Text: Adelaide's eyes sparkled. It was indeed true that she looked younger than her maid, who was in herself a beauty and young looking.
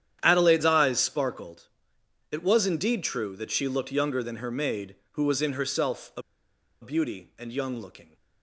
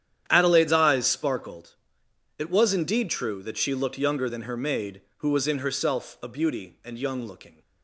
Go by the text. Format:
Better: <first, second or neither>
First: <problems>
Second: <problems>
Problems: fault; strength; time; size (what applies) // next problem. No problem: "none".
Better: second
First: starts louder than the rest; strong; until 1.2 s; 10 dB // pauses between "a" and "beauty"; noticeable; at 6.2 s; 0.59 s long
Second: starts louder than the rest; strong; until 1.2 s; 10 dB